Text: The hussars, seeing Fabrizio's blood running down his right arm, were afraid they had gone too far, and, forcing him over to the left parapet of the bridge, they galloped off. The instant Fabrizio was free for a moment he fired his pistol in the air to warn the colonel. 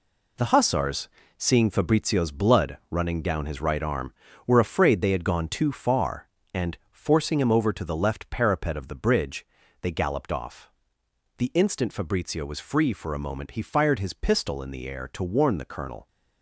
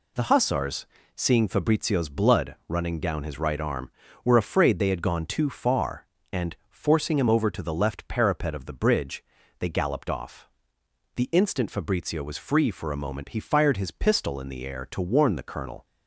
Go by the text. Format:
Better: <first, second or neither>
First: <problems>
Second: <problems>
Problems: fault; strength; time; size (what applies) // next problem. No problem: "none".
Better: second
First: gets quieter; strong; throughout; 8 dB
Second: none